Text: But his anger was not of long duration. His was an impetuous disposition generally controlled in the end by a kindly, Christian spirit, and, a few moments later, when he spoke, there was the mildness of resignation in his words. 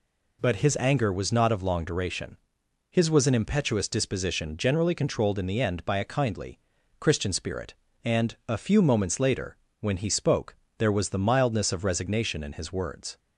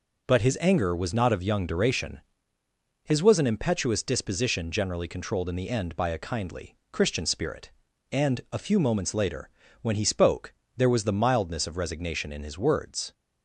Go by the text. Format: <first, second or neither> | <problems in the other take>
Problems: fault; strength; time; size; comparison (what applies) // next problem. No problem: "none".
first | says "young" for "long"; at 1.4 s